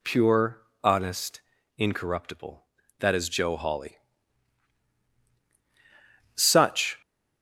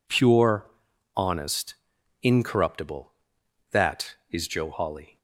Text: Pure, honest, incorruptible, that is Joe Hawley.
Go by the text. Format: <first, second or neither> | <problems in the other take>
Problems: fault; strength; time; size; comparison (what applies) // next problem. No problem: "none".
second | goes on to say "Such"; noticeable; from 6.3 s on; 0.66 s long